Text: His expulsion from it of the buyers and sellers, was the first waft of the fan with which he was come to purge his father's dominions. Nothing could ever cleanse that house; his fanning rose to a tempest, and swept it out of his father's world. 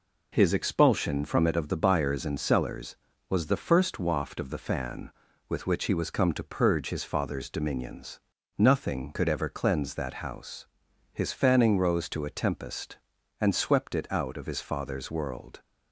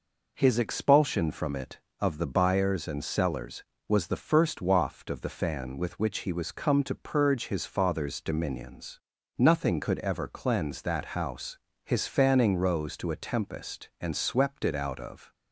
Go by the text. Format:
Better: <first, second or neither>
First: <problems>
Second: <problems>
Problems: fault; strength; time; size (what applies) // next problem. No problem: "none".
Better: first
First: none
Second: stops before "his father's world"; at 15.3 s